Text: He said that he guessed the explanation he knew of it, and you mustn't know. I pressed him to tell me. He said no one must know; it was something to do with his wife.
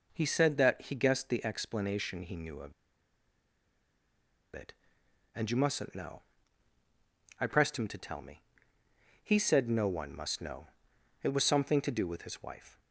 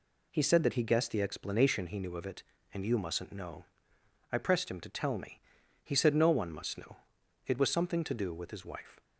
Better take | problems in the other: second | pauses between "of" and "it"; strong; at 2.7 s; 1.8 s long

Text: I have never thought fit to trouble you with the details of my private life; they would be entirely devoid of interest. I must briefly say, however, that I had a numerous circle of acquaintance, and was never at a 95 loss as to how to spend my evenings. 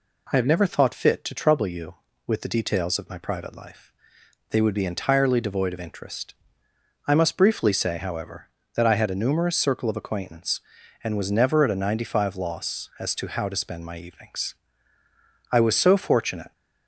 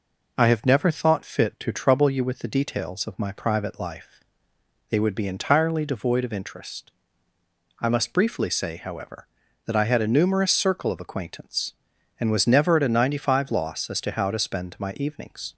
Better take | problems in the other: second | goes on to say "I was so fortunate"; noticeable; from 15.4 s on; 1.0 s long

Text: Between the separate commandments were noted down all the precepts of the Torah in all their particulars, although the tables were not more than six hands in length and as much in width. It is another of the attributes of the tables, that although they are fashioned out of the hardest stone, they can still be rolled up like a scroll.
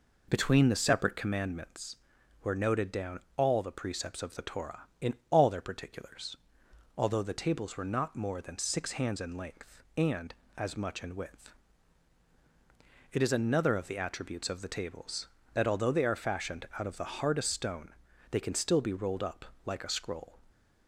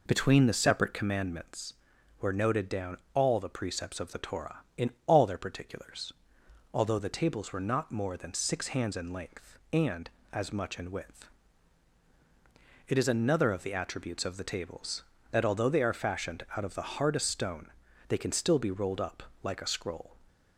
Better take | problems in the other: neither | pauses between "down" and "all"; slight; the same in both // pauses between "in" and "all"; slight; the same in both // pauses between "up" and "like"; slight; the same in both

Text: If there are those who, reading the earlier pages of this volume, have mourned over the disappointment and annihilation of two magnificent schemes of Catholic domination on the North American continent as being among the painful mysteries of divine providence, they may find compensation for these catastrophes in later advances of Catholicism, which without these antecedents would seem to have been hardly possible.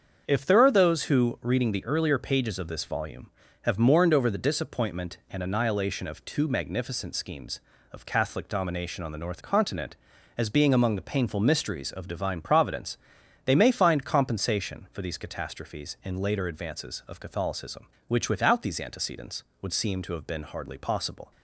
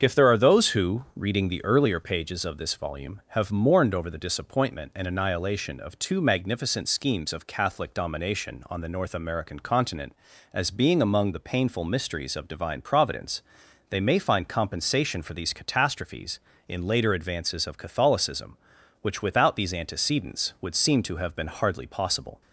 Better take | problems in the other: second | starts louder than the rest; until 1.3 s; 6.5 dB; also in the second // skips "American"; at 9.4 s

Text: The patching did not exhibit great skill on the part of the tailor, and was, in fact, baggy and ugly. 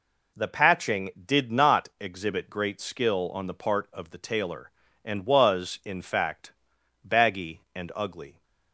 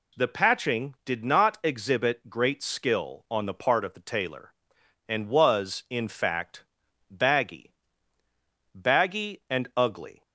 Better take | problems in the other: first | says "baggy" twice; at 8.7 s

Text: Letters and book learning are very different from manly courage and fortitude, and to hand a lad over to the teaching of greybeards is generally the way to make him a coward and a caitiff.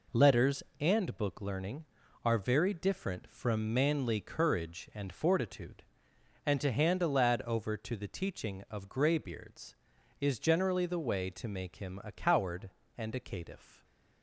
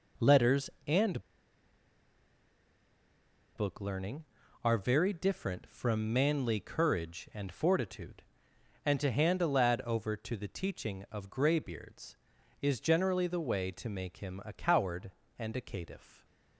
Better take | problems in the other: first | pauses between "and" and "book"; strong; at 1.2 s; 2.3 s long

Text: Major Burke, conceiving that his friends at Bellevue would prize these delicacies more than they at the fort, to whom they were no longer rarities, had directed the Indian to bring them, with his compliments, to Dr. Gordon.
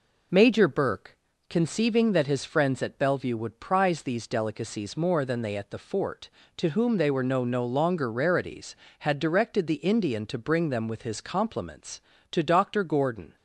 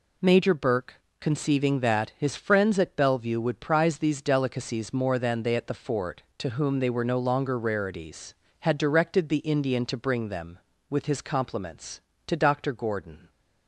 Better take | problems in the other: second | says "no" twice; at 7.4 s

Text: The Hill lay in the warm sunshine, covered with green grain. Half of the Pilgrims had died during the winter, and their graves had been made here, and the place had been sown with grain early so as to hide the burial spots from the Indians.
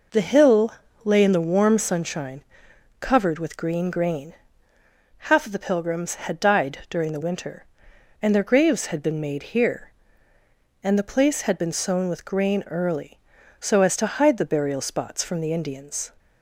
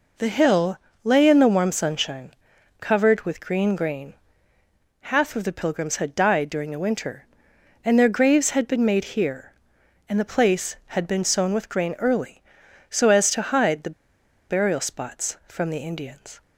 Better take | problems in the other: first | pauses between "Hill" and "lay"; slight; at 0.7 s; 0.26 s long; slight in the first // pauses between "the" and "burial"; noticeable; at 13.9 s; 0.57 s long

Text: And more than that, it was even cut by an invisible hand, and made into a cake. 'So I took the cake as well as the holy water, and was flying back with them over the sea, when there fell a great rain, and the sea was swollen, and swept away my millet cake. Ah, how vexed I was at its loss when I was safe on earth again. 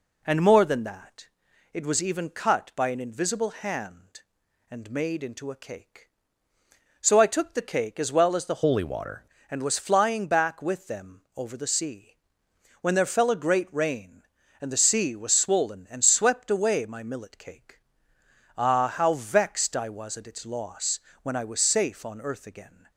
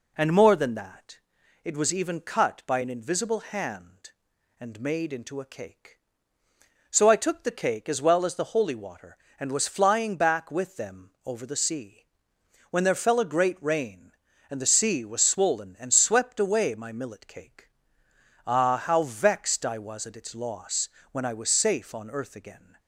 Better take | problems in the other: second | changes voice from "holy" to "water"; from 8.6 to 9.2 s; 0.6 s long // pauses between "loss" and "when"; slight; at 20.9 s; 0.22 s long; slight in the second

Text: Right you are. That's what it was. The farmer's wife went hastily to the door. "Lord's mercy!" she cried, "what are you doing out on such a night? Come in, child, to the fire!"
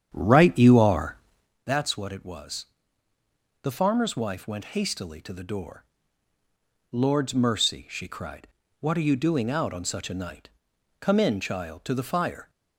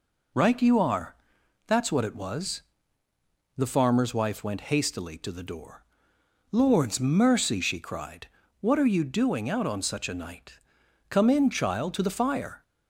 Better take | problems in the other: second | starts louder than the rest; strong; until 1.5 s; 8.5 dB

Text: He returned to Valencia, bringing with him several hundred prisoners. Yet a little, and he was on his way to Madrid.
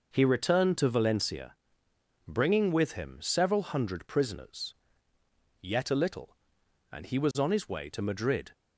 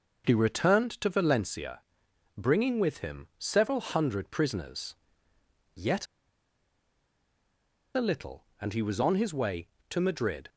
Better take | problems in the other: first | starts louder than the rest; until 1.3 s; 6.5 dB // pauses between "Yet" and "a"; strong; at 6.0 s; 1.9 s long

